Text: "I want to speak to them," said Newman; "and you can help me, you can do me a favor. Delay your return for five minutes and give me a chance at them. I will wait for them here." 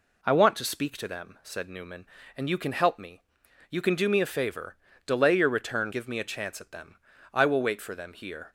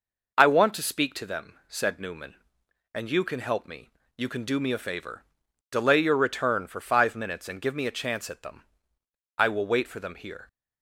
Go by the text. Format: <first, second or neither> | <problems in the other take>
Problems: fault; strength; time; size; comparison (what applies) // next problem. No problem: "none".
second | skips "for five minutes and"; at 5.9 s